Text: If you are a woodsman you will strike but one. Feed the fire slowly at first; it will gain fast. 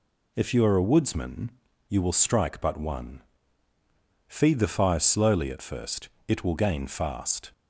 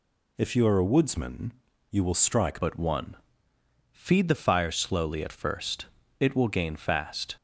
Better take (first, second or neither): first